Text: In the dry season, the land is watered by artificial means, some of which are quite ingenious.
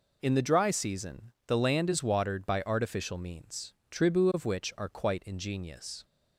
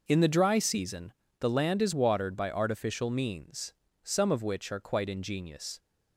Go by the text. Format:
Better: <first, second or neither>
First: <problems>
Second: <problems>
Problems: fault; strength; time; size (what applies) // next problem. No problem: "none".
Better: second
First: says "tribu" for "some"; at 3.8 s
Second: none